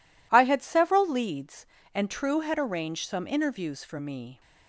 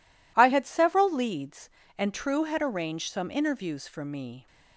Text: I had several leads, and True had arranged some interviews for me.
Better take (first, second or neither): neither